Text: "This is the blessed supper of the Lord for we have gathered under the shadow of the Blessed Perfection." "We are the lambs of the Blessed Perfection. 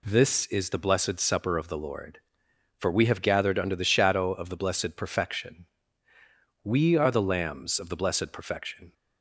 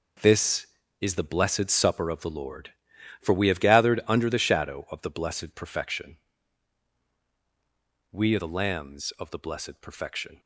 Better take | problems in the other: first | gets quieter; strong; throughout; 11.5 dB

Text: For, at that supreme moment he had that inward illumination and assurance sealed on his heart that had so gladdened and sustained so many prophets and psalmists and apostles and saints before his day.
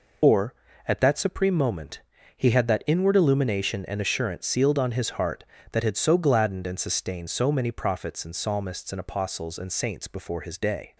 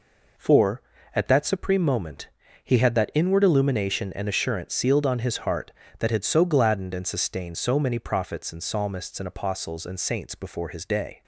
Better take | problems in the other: second | loses the start of "For"; at 0.2 s; 130 ms // pauses between "moment" and "he"; slight; at 1.9 s; 0.36 s long; slight in the second

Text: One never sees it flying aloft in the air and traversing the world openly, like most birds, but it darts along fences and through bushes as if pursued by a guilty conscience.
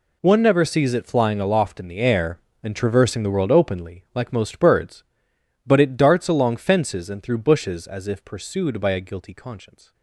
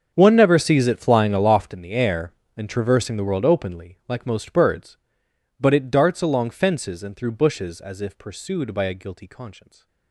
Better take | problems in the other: first | starts louder than the rest; until 1.8 s; 7 dB

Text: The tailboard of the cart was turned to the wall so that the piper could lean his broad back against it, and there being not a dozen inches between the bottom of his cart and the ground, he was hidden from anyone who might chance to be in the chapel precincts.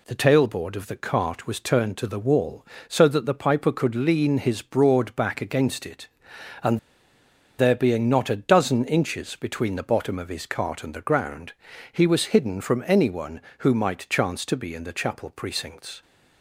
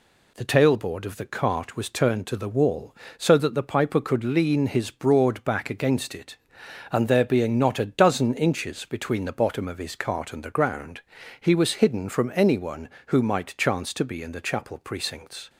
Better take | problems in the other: second | pauses between "and" and "there"; noticeable; at 6.7 s; 0.79 s long

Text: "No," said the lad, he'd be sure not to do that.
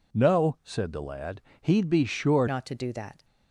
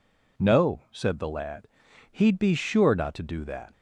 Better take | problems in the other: second | changes voice at "not"; from 2.4 s on; 0.8 s long

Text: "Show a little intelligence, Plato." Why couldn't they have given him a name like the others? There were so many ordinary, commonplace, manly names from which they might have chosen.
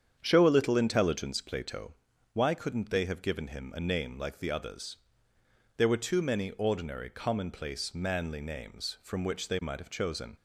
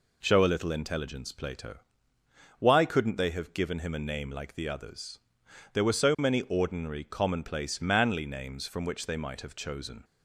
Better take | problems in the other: second | starts louder than the rest; strong; until 1.2 s; 8 dB // says "too" for "so"; at 5.9 s

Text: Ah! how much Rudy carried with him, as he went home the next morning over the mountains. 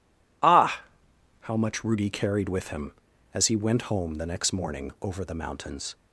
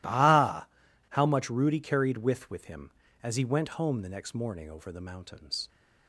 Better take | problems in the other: first | says "with" twice; at 2.4 s

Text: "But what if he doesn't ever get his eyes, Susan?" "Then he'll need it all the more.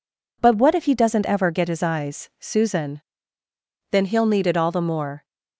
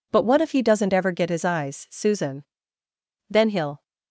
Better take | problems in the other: first | stops before "need it all the more"; at 3.8 s

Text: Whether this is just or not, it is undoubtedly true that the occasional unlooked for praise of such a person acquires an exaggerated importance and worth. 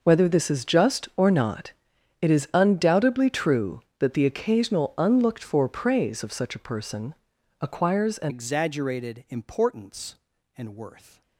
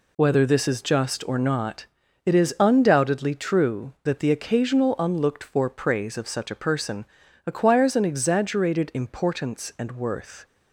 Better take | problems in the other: second | pauses between "person" and "acquires"; noticeable; at 7.1 s; 0.48 s long; also in the second // changes voice at "exaggerated"; from 8.2 s on; 3.0 s long

